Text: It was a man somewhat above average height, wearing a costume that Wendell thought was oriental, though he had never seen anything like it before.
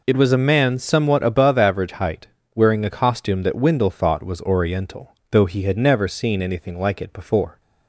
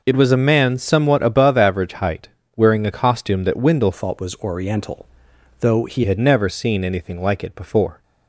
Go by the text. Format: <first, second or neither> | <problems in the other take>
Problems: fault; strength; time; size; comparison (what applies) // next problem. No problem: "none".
first | changes voice from "thought" to "he"; from 3.9 to 6.0 s; 2.1 s long